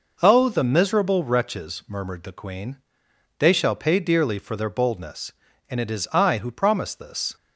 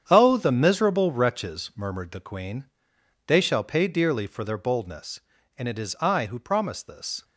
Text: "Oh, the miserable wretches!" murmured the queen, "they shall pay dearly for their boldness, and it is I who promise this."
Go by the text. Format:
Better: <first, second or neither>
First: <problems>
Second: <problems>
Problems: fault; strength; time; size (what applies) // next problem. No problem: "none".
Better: first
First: none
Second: gets quieter; strong; throughout; 10 dB